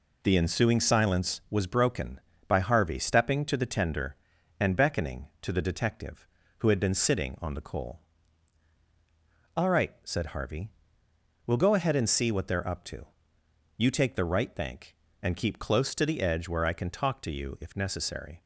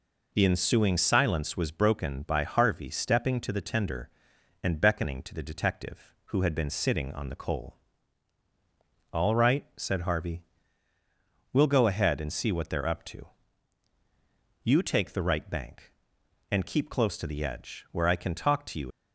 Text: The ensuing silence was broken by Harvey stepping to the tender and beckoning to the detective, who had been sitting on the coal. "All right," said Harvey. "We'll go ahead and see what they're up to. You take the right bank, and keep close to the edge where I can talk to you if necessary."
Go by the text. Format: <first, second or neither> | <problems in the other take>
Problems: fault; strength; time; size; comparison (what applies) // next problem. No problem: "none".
first | stops before "if necessary"; at 18.9 s